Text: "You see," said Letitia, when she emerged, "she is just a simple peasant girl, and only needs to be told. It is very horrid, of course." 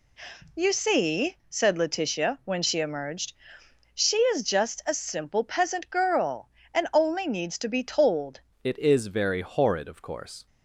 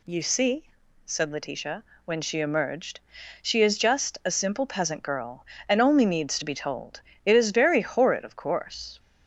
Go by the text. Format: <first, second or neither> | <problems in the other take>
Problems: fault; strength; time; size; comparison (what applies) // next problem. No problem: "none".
second | changes voice at "It"; from 8.6 s on; 1.8 s long